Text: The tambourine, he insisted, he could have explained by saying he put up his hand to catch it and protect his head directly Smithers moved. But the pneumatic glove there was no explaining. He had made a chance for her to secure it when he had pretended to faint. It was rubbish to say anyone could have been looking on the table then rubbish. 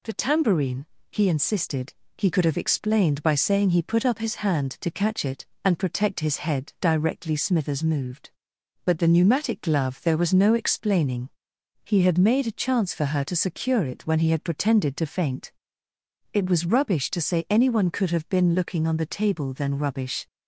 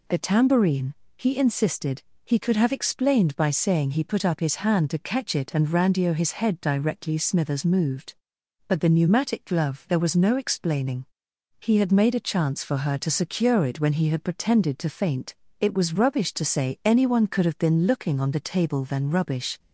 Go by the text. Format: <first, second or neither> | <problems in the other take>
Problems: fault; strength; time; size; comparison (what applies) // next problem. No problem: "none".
first | says "randio" for "protect"; at 5.6 s